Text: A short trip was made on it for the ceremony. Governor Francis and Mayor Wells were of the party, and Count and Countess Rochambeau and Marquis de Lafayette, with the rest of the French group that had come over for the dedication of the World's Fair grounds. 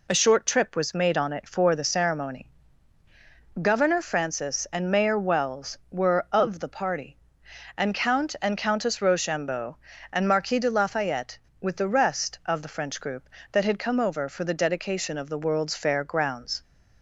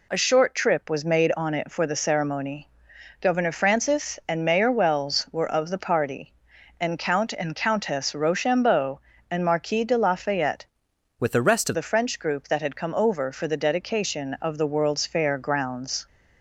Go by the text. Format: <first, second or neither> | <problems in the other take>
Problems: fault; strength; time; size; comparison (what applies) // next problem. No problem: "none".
first | changes voice from "with" to "of"; from 11.1 to 11.7 s; 0.6 s long